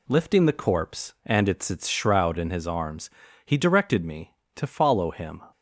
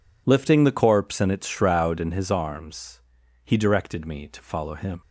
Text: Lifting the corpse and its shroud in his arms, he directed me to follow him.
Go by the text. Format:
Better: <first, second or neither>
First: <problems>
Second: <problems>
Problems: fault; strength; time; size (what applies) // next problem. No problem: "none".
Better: second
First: says "its" twice; at 1.6 s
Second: none